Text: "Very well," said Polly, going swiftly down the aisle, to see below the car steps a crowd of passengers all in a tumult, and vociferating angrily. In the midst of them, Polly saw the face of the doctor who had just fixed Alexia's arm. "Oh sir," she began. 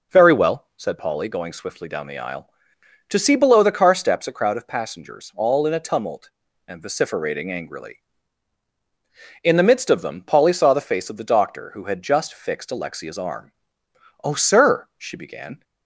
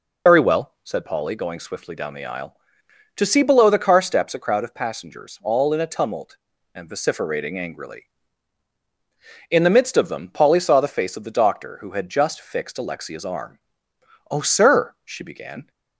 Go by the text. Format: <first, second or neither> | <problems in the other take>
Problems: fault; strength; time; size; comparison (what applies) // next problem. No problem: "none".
first | loses the start of "Very"; at 0.2 s; 80 ms